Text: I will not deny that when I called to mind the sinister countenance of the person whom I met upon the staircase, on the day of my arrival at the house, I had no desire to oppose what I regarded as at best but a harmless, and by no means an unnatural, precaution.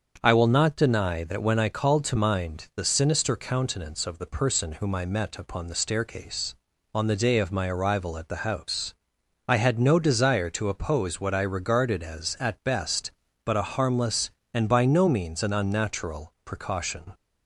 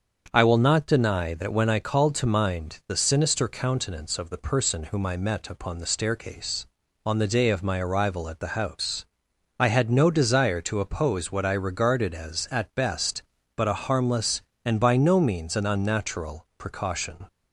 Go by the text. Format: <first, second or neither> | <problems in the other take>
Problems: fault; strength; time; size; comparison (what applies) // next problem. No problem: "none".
neither | starts louder than the rest; the same in both